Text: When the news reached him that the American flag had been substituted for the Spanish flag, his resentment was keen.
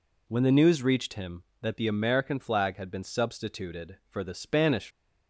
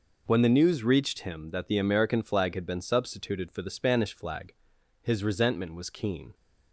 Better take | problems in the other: second | stops before "flag his resentment was keen"; at 4.9 s

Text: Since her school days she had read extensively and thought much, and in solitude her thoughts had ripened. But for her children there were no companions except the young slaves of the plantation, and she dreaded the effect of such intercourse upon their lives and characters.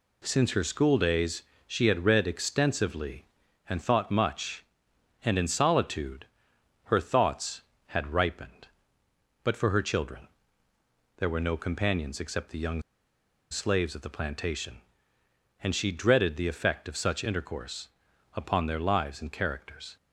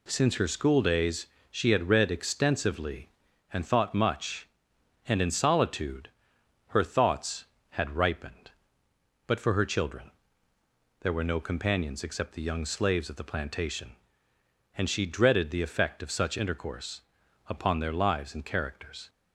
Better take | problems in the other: second | pauses between "days" and "she"; slight; at 1.4 s; 0.24 s long; slight in the second // pauses between "solitude" and "her"; noticeable; at 6.2 s; 0.58 s long; noticeable in the second // pauses between "children" and "there"; noticeable; at 10.2 s; 0.88 s long; noticeable in the second // pauses between "young" and "slaves"; noticeable; at 12.8 s; 0.70 s long // pauses between "intercourse" and "upon"; noticeable; at 17.8 s; 0.46 s long; noticeable in the second

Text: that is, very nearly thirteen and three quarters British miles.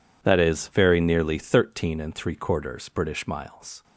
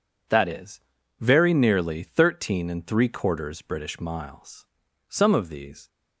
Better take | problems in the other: first | goes on to say "Some of these"; noticeable; from 5.0 s on; 0.80 s long

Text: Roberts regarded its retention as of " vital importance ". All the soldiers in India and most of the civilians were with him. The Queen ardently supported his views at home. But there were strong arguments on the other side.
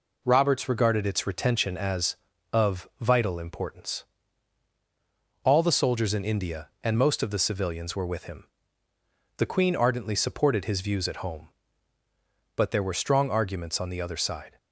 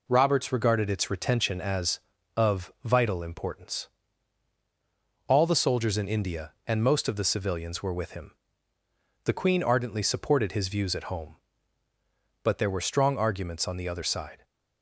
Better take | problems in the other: neither | none

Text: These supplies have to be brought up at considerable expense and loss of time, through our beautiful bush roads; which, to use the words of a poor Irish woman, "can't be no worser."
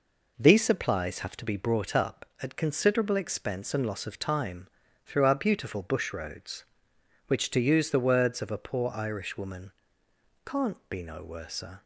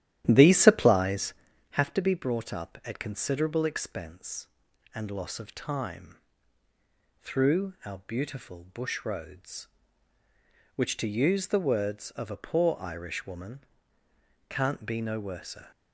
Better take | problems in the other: first | starts louder than the rest; strong; until 1.7 s; 12 dB

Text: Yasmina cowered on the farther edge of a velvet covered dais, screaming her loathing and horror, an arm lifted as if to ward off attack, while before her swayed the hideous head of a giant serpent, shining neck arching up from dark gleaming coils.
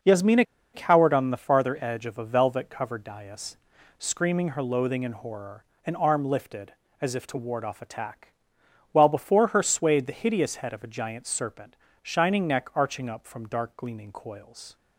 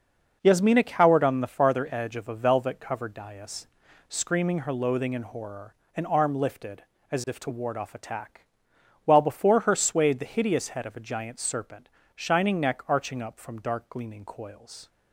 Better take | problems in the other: second | pauses between "Yasmina" and "cowered"; slight; at 0.4 s; 0.31 s long

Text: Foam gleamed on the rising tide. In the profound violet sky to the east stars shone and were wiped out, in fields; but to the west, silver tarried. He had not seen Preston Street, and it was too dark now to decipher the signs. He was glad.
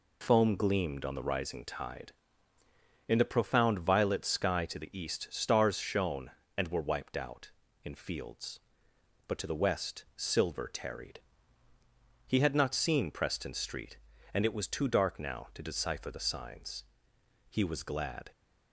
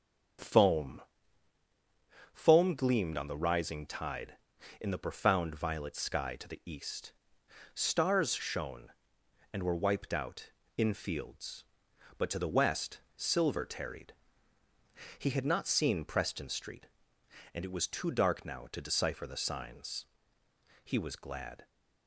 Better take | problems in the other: first | starts louder than the rest; strong; until 2.7 s; 7 dB // says "Foam" twice; at 2.3 s // pauses between "east" and "stars"; noticeable; at 7.1 s; 0.60 s long

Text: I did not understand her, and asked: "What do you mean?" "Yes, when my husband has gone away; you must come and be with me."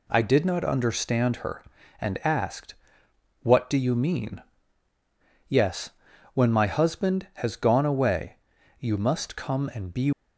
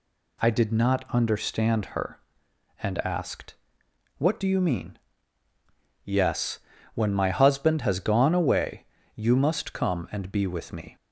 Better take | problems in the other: second | stops before "with me"; at 10.1 s

